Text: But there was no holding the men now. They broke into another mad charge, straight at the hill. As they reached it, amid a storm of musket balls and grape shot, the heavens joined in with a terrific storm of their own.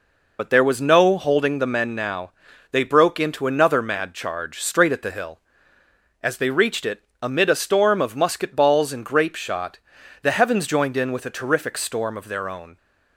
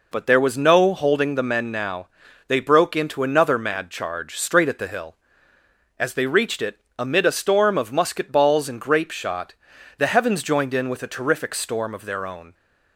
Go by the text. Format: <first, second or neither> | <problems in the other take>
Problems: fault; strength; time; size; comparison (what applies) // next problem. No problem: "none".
second | loses the start of "But"; at 0.3 s; 30 ms